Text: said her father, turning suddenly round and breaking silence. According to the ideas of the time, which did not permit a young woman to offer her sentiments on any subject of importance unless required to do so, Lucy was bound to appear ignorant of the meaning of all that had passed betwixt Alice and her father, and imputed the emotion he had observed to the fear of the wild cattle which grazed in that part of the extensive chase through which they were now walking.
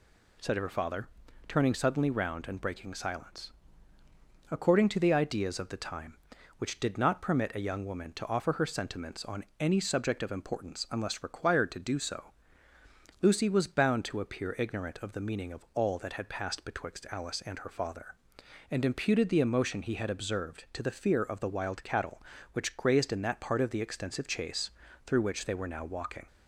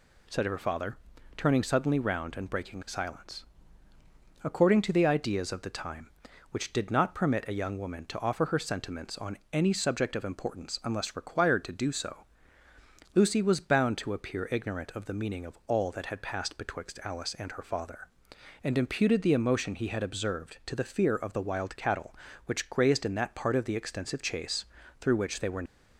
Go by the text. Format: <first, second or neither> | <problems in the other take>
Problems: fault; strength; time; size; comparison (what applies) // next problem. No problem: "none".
first | pauses between "on" and "any"; slight; at 9.3 s; 0.16 s long; slight in the first // pauses between "chase" and "through"; slight; at 24.6 s; 0.34 s long; slight in the first // stops before "now walking"; at 25.6 s